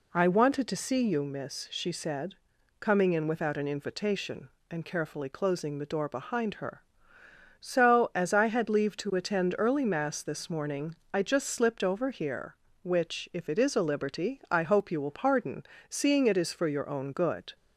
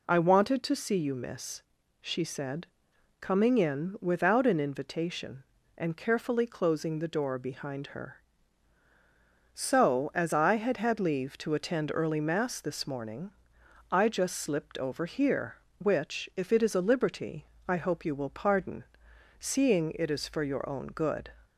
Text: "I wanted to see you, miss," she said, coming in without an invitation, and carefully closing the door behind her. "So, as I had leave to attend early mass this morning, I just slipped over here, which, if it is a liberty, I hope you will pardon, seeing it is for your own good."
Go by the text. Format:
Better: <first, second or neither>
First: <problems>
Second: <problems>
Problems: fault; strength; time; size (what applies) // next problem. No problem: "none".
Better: first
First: none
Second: says "had" twice; at 10.7 s